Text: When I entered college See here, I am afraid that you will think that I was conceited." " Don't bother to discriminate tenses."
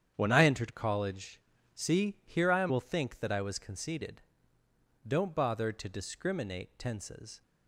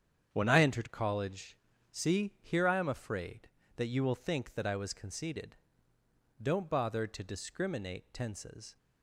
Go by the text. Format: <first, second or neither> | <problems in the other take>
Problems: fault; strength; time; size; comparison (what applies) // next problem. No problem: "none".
second | starts louder than the rest; strong; until 1.1 s; 9.5 dB; strong in the second // pauses between "college" and "See"; slight; at 1.4 s; 0.34 s long; slight in the second // skips "afraid that you"; at 2.6 s